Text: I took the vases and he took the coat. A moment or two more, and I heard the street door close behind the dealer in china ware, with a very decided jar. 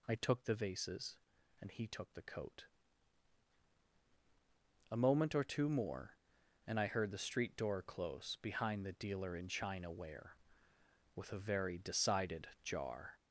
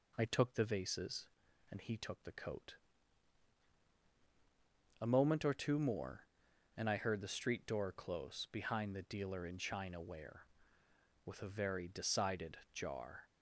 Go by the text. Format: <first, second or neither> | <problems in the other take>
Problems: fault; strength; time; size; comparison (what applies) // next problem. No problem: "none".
second | gets louder; noticeable; throughout; 6 dB